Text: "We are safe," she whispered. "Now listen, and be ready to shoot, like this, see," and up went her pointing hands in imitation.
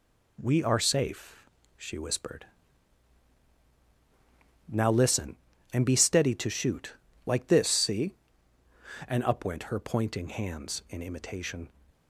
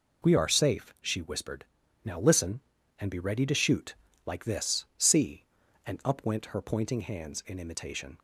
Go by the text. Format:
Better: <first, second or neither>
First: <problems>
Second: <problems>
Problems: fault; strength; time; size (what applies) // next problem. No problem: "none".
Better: second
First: says "steady" for "ready"; at 5.9 s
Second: none